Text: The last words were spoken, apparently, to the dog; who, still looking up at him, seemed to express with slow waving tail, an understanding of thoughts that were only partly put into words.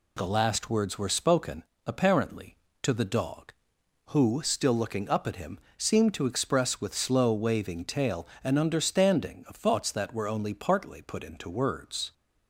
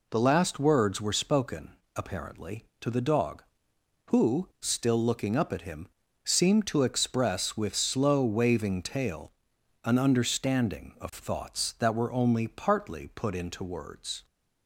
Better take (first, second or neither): neither